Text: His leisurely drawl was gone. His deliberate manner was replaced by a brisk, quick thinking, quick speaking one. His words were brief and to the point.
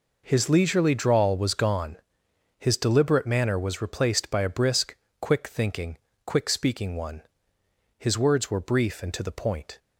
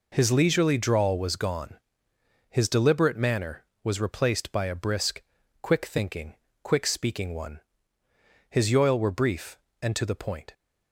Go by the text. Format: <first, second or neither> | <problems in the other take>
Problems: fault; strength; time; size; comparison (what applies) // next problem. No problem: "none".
first | says "yoil" for "words"; at 8.7 s